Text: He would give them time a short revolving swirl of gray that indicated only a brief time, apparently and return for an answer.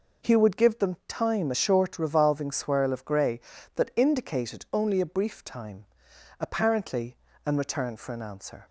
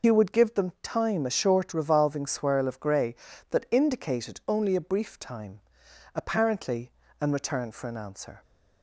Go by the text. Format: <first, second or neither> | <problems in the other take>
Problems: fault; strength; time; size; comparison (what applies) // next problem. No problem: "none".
first | loses the start of "He"; at 0.0 s; 65 ms